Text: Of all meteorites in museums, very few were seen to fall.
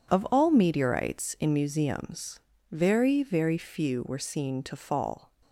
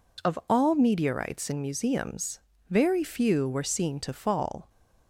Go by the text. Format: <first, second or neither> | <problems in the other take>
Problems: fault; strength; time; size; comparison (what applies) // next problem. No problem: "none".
second | says "very" twice; at 3.2 s